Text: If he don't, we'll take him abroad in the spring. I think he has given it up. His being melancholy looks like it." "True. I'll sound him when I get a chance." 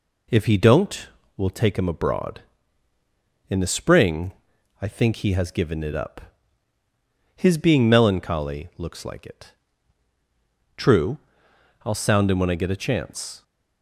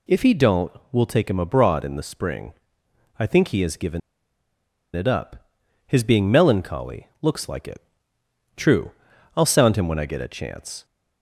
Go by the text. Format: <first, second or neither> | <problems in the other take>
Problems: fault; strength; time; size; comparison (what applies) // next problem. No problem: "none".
first | pauses between "given" and "it"; noticeable; at 4.0 s; 0.94 s long // pauses between "melancholy" and "looks"; slight; at 7.0 s; 0.16 s long